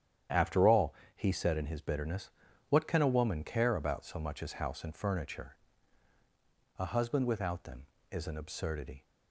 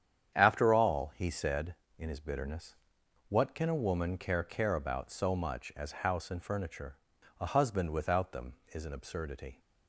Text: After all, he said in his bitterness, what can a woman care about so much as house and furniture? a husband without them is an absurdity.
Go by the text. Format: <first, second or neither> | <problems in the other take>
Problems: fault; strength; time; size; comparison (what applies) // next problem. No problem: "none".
first | starts louder than the rest; strong; until 1.3 s; 9 dB; strong in the first // says "care" twice; at 4.4 s